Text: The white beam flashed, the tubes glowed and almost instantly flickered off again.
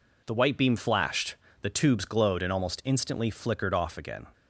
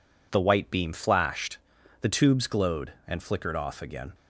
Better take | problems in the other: first | skips "almost instantly"; at 3.1 s

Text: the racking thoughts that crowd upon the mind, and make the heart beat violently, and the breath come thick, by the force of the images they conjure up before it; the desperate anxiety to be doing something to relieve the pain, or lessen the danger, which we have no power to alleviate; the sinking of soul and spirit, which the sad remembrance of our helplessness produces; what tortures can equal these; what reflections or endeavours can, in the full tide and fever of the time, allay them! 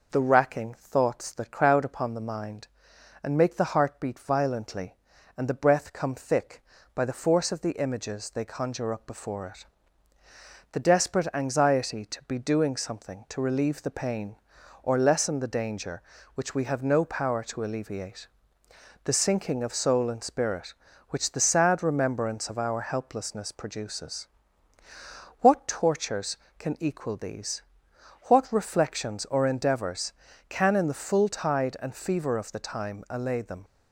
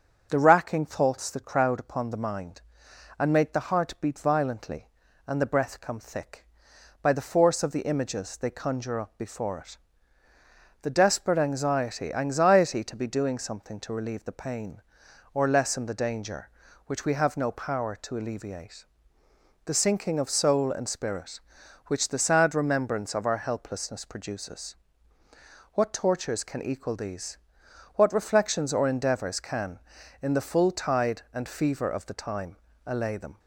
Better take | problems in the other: first | starts louder than the rest; strong; until 1.3 s; 7.5 dB // says "anxiety" twice; at 12.1 s

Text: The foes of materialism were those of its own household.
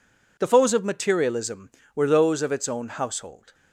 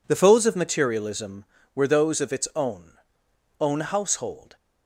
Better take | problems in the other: first | says "own" twice; at 3.5 s

